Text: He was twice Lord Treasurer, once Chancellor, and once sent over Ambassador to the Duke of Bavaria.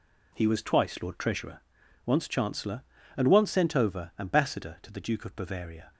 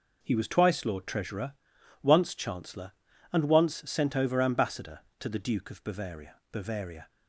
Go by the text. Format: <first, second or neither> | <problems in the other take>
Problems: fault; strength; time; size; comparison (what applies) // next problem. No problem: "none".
first | says "Bavaria" twice; at 6.5 s